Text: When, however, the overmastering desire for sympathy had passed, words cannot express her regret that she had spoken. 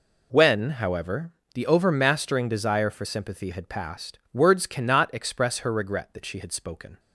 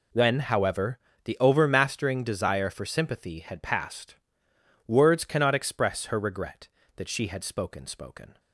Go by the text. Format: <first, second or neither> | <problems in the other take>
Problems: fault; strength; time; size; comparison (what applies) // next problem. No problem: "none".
first | says "spoken" twice; at 7.8 s